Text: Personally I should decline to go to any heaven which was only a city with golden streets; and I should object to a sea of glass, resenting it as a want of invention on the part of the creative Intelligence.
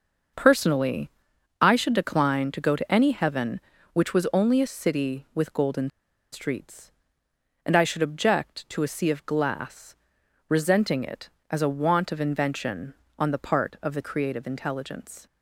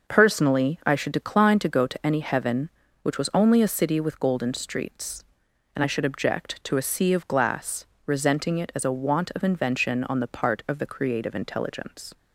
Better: second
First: starts louder than the rest; noticeable; until 1.8 s; 6 dB // pauses between "Personally" and "I"; noticeable; at 1.0 s; 0.52 s long // pauses between "golden" and "streets"; at 5.8 s; 0.43 s long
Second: none

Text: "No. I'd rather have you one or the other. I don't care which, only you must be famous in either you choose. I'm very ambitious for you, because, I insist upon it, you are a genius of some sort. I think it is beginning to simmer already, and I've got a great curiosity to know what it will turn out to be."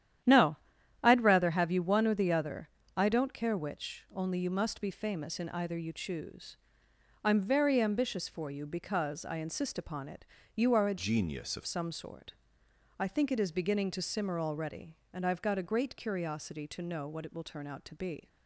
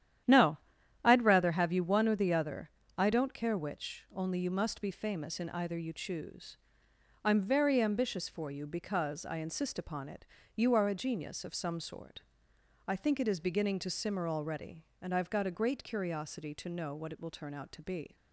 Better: second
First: starts louder than the rest; strong; until 1.7 s; 10.5 dB // changes voice from "genius" to "of"; from 10.9 to 11.6 s; 0.7 s long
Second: starts louder than the rest; strong; until 1.7 s; 10.5 dB

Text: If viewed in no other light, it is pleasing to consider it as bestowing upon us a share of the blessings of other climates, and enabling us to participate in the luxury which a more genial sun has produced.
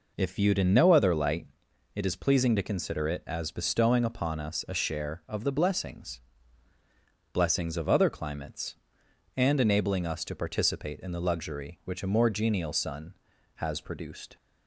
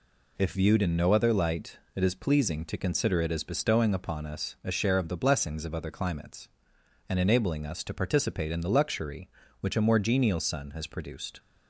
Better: second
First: says "blessings" twice; at 7.3 s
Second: none

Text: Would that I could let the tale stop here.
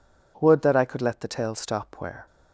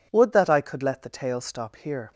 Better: second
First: says "where" for "here"; at 1.9 s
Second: none

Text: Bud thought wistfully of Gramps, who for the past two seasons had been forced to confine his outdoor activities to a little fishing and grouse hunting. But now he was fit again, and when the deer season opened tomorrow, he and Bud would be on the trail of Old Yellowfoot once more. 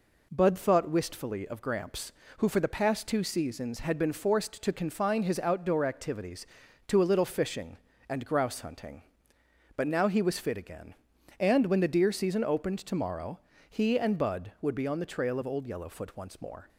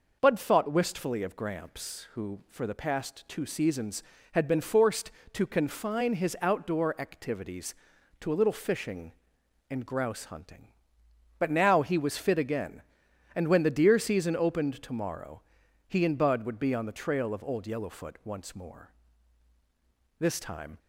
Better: first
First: none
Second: goes on to say "This time"; from 20.2 s on; 0.58 s long

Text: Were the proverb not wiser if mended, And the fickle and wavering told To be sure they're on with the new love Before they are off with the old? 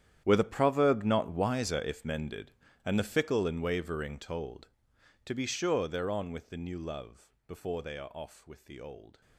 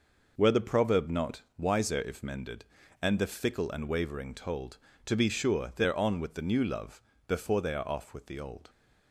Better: second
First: gets quieter; strong; throughout; 17.5 dB // pauses between "love" and "Before"; slight; at 7.3 s; 0.16 s long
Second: pauses between "love" and "Before"; slight; at 7.0 s; 0.26 s long

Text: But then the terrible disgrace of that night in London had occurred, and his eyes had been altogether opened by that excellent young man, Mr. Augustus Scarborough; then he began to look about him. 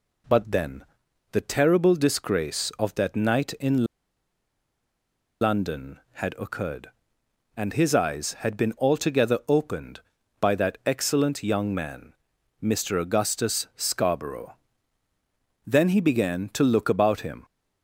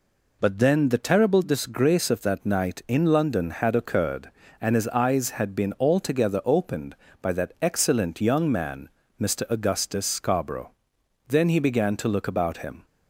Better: second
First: pauses between "then" and "the"; noticeable; at 0.8 s; 0.48 s long // pauses between "in" and "London"; strong; at 3.8 s; 1.5 s long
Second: none

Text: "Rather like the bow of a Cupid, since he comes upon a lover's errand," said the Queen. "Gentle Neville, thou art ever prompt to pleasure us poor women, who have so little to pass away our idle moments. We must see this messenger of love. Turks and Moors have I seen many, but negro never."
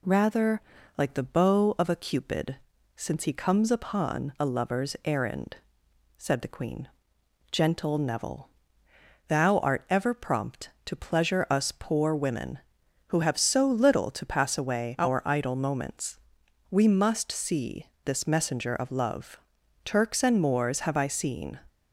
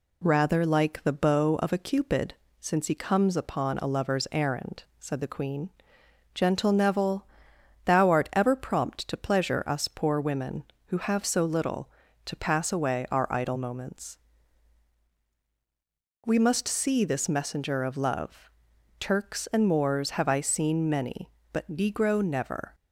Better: second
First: pauses between "Rather" and "like"; at 0.6 s; 0.38 s long // pauses between "see" and "this"; slight; at 17.8 s; 0.18 s long // stops before "many but negro never"; at 21.6 s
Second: none

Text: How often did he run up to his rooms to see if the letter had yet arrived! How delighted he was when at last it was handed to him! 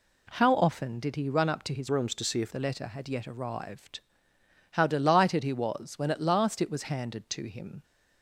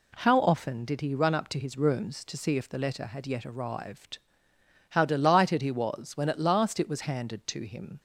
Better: second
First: changes voice from "rooms" to "if"; from 1.8 to 2.5 s; 0.7 s long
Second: none

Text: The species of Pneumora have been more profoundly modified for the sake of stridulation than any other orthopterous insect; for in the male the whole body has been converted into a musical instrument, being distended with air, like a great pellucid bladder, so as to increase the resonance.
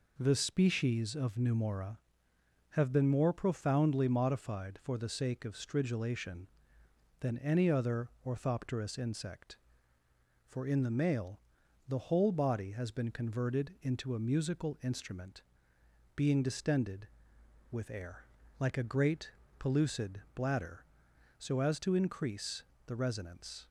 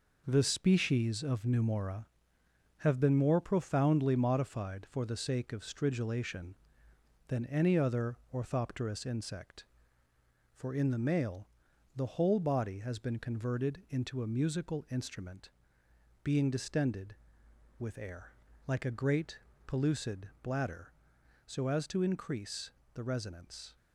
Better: first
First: pauses between "other" and "orthopterous"; slight; at 8.0 s; 0.18 s long // pauses between "male" and "the"; at 11.4 s; 0.44 s long // pauses between "great" and "pellucid"; slight; at 19.3 s; 0.26 s long // pauses between "increase" and "the"; slight; at 22.6 s; 0.22 s long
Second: gets quieter; throughout; 6.5 dB // pauses between "other" and "orthopterous"; slight; at 8.1 s; 0.18 s long // pauses between "male" and "the"; at 11.4 s; 0.44 s long // pauses between "great" and "pellucid"; slight; at 19.3 s; 0.26 s long // pauses between "increase" and "the"; slight; at 22.7 s; 0.22 s long

